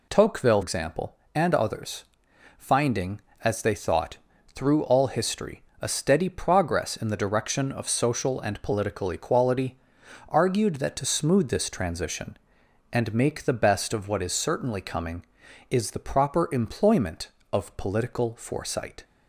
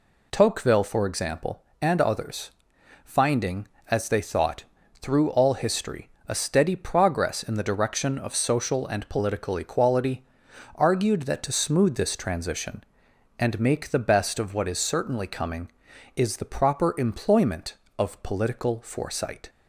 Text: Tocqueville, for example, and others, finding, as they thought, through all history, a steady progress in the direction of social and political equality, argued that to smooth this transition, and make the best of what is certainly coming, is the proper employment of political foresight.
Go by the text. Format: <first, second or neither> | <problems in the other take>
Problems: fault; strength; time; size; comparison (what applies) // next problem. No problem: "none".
second | skips "for"; at 0.6 s